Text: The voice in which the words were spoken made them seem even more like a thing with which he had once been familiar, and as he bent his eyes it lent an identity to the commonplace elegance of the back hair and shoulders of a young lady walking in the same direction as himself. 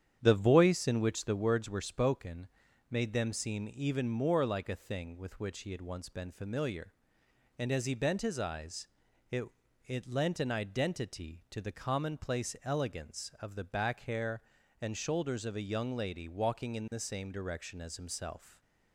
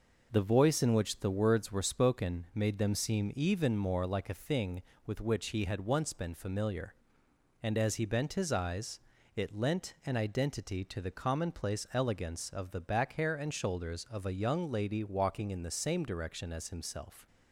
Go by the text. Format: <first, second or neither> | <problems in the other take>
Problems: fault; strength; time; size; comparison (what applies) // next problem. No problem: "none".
second | starts louder than the rest; strong; until 1.2 s; 9.5 dB // pauses between "spoken" and "made"; at 2.4 s; 0.42 s long // pauses between "eyes" and "it"; at 8.8 s; 0.42 s long; slight in the second // says "it" twice; at 9.8 s